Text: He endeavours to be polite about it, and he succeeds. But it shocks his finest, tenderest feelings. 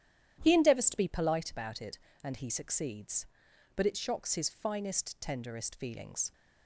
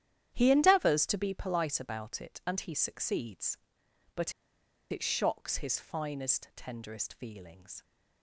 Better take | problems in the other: first | starts louder than the rest; strong; until 1.3 s; 10.5 dB; strong in the first // pauses between "But" and "it"; noticeable; at 4.3 s; 0.60 s long

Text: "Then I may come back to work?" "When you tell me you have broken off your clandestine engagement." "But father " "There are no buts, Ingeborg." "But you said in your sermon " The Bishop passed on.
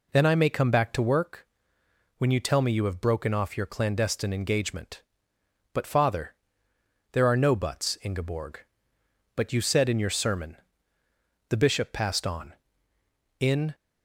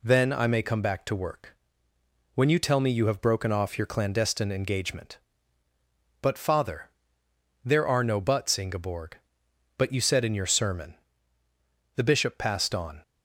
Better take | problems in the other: second | goes on to say "In"; slight; from 13.3 s on; 0.36 s long

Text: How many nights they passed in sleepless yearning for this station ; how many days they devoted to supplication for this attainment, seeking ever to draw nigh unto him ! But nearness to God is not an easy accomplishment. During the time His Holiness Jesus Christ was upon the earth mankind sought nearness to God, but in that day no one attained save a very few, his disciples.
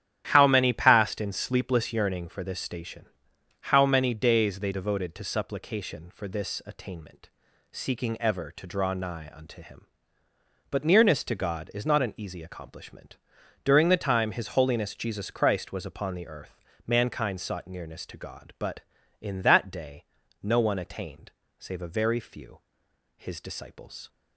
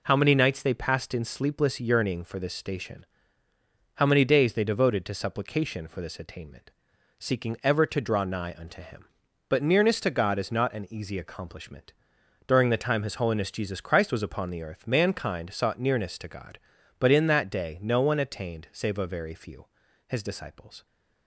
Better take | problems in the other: second | starts louder than the rest; strong; until 1.3 s; 11.5 dB // skips "nights they"; at 0.7 s // pauses between "earth" and "mankind"; slight; at 16.5 s; 0.30 s long // pauses between "day" and "no"; at 20.0 s; 0.38 s long // pauses between "attained" and "save"; slight; at 21.3 s; 0.26 s long

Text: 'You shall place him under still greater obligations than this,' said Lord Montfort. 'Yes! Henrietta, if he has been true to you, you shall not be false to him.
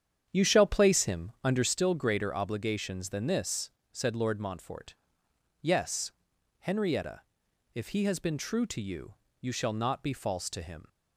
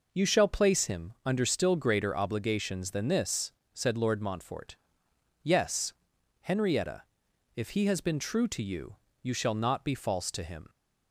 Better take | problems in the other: second | starts louder than the rest; strong; until 1.8 s; 8.5 dB

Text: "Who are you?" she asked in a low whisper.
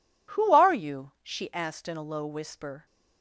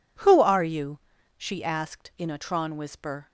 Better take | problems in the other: first | says "tron" for "low"; at 2.3 s

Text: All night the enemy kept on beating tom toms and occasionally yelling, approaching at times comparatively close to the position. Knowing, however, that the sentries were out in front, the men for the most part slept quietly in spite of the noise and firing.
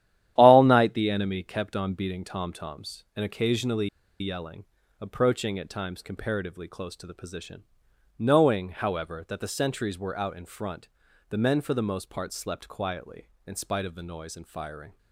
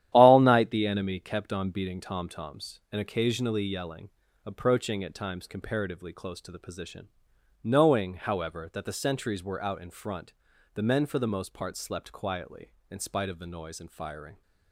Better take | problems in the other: second | starts louder than the rest; strong; until 1.3 s; 11.5 dB; strong in the second // pauses between "occasionally" and "yelling"; slight; at 3.8 s; 0.33 s long

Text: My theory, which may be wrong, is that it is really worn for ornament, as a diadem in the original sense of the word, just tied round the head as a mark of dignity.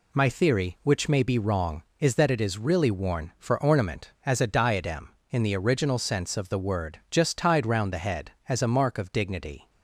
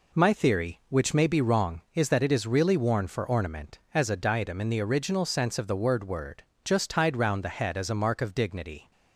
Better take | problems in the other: first | says "word" twice; at 6.0 s

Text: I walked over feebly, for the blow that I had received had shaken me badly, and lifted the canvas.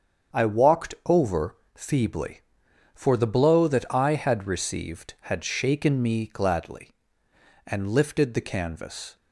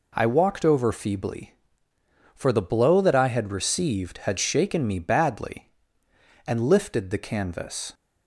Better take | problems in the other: second | starts louder than the rest; strong; until 1.4 s; 7.5 dB // pauses between "over" and "feebly"; slight; at 1.5 s; 0.18 s long // says "gladly" for "badly"; at 6.2 s

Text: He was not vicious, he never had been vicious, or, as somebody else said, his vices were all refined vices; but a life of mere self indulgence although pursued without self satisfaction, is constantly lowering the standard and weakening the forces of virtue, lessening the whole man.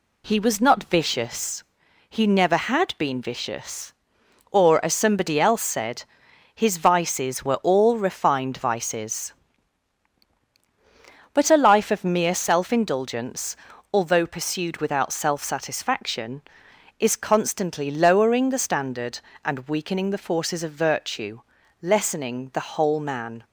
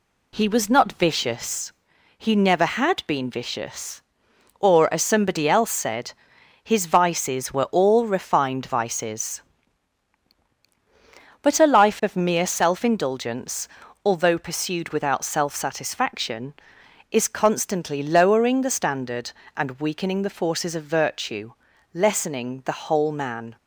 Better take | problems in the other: neither | pauses between "indulgence" and "although"; the same in both

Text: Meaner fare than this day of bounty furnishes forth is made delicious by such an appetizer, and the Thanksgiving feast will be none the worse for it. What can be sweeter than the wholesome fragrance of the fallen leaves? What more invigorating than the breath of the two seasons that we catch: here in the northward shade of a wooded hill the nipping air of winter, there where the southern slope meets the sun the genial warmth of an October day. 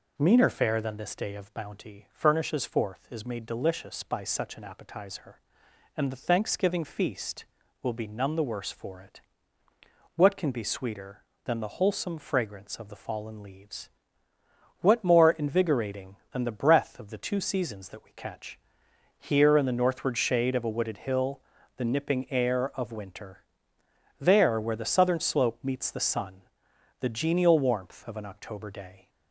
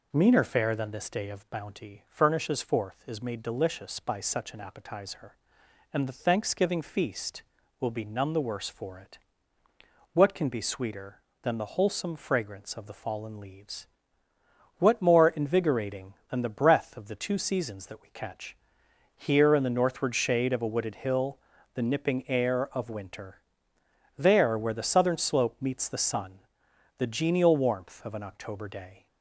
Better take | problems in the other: neither | pauses between "hill" and "the"; slight; the same in both // pauses between "sun" and "the"; noticeable; the same in both

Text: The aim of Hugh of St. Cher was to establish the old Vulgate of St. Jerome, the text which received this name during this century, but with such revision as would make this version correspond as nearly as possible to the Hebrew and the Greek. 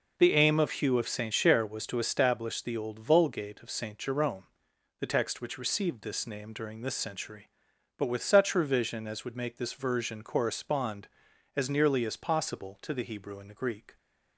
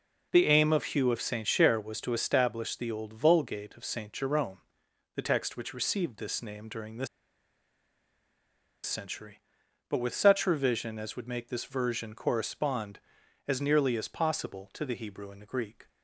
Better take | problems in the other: first | pauses between "this" and "century"; strong; at 7.0 s; 1.7 s long

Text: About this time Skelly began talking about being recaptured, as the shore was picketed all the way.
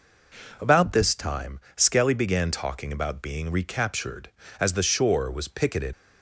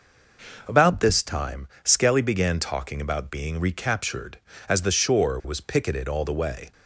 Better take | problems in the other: second | pauses between "time" and "Skelly"; slight; at 1.6 s; 0.16 s long; slight in the second // stops before "all the way"; at 5.9 s

